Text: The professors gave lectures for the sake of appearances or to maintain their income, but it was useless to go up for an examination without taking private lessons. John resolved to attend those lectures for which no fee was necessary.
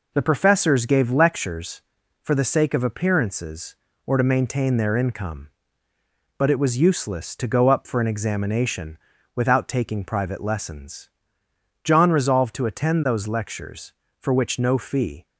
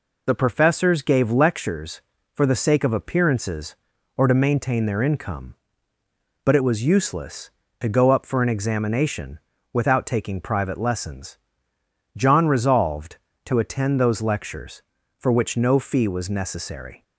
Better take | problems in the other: second | pauses between "examination" and "without"; slight; at 8.9 s; 0.36 s long; slight in the second // stops before "was necessary"; at 15.2 s

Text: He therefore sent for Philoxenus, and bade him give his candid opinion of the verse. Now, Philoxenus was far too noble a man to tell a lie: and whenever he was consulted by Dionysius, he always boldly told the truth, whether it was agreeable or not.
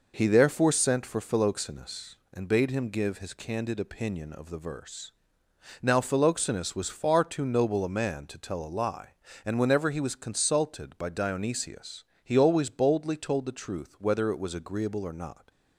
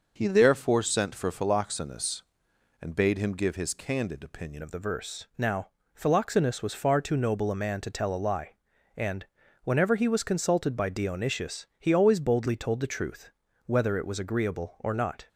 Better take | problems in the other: first | changes voice at "of"; from 4.6 s on; 10.6 s long // pauses between "and" and "whenever"; at 9.2 s; 0.40 s long

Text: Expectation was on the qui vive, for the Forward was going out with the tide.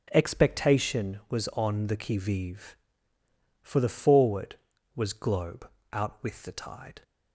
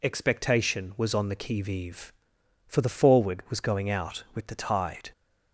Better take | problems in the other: second | says "globe" for "going"; at 5.1 s

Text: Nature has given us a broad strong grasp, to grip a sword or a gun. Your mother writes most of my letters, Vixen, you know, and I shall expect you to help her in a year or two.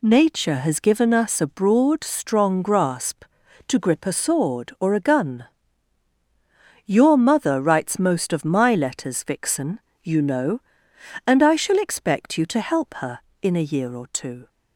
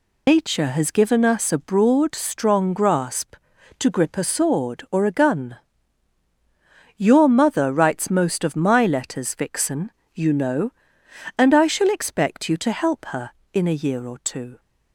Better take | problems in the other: first | loses the start of "Nature"; at 0.2 s; 135 ms

